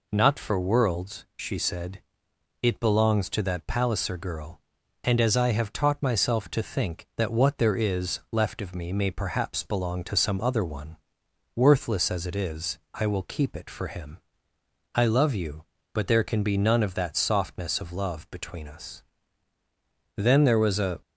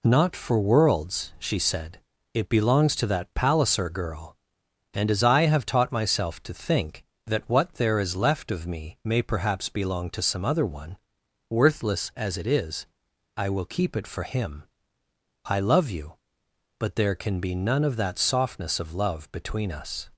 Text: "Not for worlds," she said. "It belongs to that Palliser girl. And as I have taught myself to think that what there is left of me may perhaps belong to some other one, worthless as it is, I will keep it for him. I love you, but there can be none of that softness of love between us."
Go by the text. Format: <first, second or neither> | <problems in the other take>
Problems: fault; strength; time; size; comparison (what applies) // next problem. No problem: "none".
second | goes on to say "Then there was a"; noticeable; from 20.1 s on; 0.86 s long